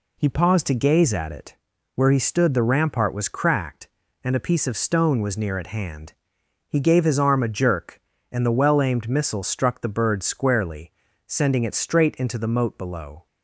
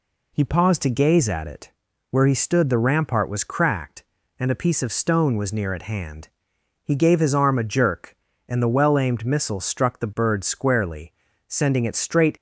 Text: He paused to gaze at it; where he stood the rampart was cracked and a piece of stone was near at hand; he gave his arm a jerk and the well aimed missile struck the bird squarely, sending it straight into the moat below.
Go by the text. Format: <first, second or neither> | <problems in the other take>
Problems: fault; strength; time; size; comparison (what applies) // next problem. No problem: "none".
first | stops before "into the moat below"; at 12.3 s